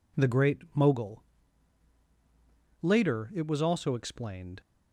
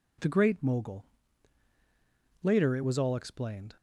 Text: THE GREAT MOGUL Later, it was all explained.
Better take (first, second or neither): second